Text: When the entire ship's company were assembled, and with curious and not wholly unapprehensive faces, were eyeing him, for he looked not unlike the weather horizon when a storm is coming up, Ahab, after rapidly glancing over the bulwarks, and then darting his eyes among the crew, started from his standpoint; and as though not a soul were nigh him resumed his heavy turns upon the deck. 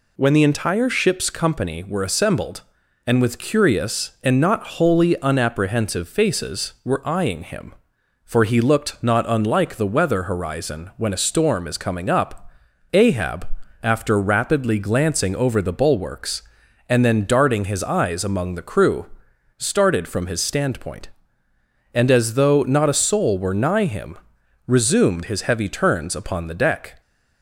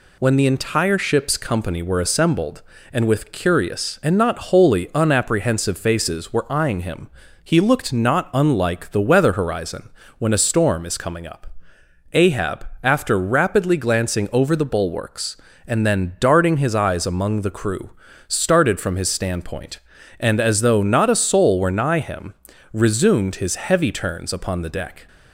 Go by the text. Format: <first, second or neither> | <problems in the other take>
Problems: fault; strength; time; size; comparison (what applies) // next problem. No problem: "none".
first | skips "for"; at 7.2 s // pauses between "horizon" and "when"; slight; at 9.8 s; 0.30 s long // pauses between "him" and "resumed"; at 22.3 s; 0.40 s long; noticeable in the first